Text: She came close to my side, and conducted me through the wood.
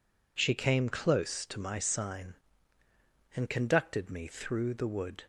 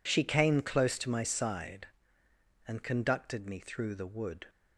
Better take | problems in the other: second | says "sign" for "side"; at 1.7 s

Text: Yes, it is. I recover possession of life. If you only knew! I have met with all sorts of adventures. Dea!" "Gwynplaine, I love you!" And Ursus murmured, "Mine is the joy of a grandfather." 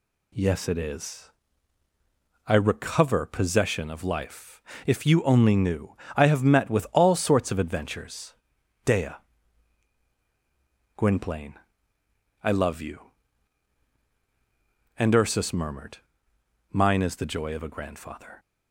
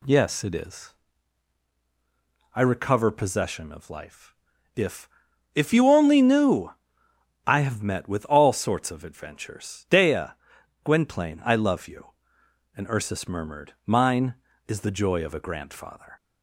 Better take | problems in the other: first | says "If" twice; at 5.5 s

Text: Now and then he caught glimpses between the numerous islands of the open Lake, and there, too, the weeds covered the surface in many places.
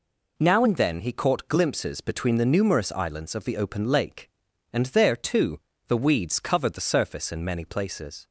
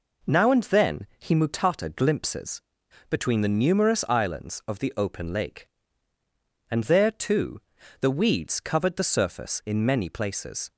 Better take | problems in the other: first | says "mutata" for "caught"; at 1.3 s // pauses between "glimpses" and "between"; noticeable; at 2.6 s; 0.50 s long

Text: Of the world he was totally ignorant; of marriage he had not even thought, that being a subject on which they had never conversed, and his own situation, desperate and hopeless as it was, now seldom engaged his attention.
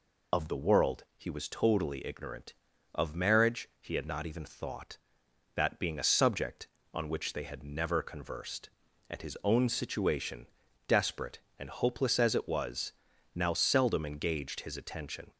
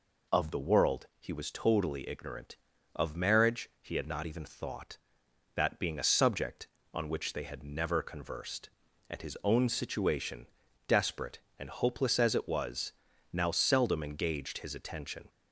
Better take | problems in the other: second | loses the start of "Of"; at 0.3 s; 60 ms

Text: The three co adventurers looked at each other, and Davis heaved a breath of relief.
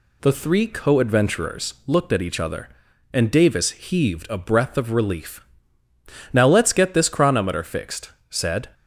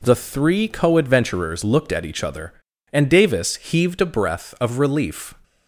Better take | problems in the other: second | goes on to say "Now let's get this chronometer fixed said"; strong; from 6.3 s on; 2.3 s long

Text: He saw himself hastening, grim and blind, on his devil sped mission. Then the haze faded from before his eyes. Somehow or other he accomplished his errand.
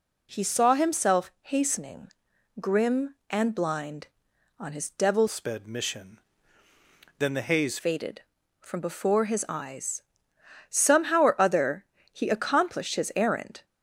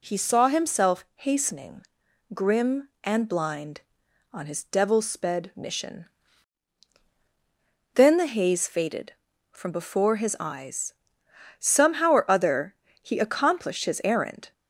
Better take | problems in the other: second | changes voice from "sped" to "haze"; from 5.2 to 7.7 s; 2.5 s long // pauses between "other" and "he"; slight; at 11.8 s; 0.26 s long; slight in the second

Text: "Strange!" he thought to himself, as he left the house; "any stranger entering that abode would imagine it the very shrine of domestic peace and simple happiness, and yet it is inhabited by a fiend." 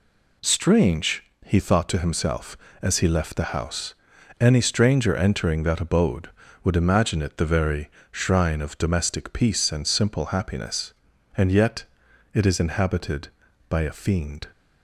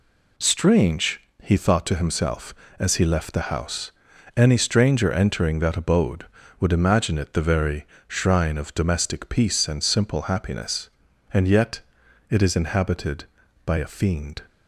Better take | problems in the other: neither | pauses between "very" and "shrine"; slight; the same in both // pauses between "yet" and "it"; noticeable; the same in both

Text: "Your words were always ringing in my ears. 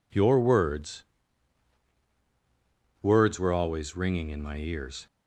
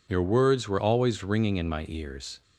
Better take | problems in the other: second | says "words" twice; at 3.0 s

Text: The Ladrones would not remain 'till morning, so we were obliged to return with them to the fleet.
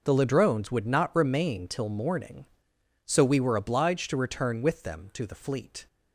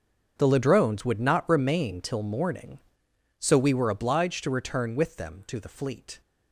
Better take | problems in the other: first | gets quieter; strong; throughout; 15.5 dB

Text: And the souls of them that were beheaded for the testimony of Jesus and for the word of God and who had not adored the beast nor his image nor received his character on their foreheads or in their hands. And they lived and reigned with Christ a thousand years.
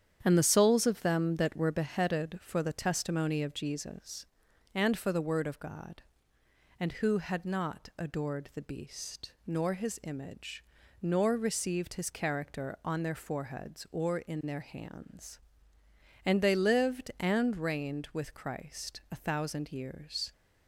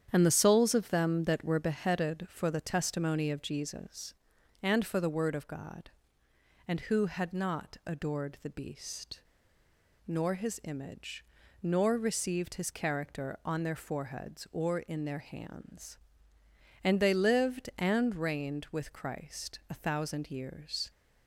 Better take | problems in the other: first | starts louder than the rest; strong; until 1.1 s; 9 dB; strong in the first // pauses between "beast" and "nor"; noticeable; at 9.2 s; 0.86 s long // pauses between "image" and "nor"; at 11.2 s; 0.38 s long; also in the first

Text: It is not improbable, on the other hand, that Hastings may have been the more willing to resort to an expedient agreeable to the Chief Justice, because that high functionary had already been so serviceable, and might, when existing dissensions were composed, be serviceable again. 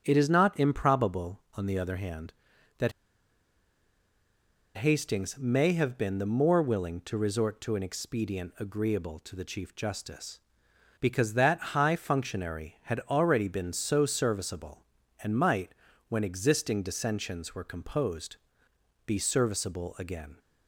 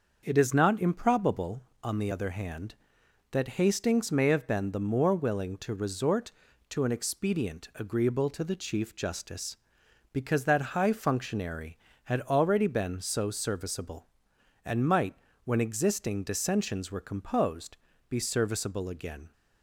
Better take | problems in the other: second | starts louder than the rest; strong; until 1.0 s; 7.5 dB; also in the second // pauses between "that" and "Hastings"; strong; at 2.9 s; 1.8 s long

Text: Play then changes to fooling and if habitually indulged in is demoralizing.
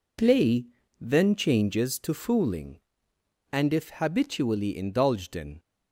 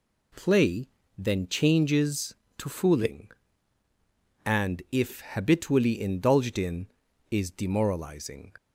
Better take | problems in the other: second | pauses between "Play" and "then"; slight; at 0.6 s; 0.35 s long; slight in the second // stops before "is demoralizing"; at 5.5 s

